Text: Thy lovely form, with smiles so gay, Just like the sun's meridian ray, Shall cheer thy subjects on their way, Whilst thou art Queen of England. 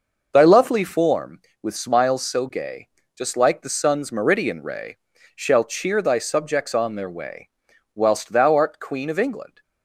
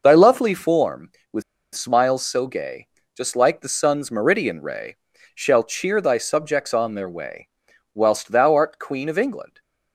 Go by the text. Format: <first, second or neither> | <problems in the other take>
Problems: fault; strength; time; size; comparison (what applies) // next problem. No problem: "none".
first | pauses between "with" and "smiles"; slight; at 1.4 s; 0.32 s long